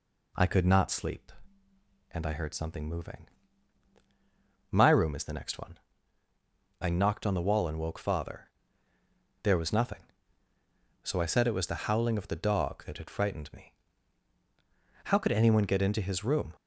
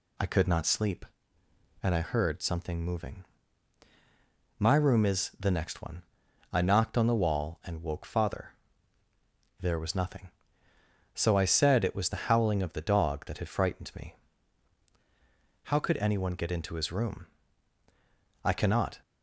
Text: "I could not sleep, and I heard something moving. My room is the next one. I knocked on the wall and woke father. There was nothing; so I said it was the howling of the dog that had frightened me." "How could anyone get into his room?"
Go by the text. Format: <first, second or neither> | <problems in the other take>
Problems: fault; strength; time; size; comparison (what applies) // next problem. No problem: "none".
first | goes on to say "I cannot"; from 18.4 s on; 0.60 s long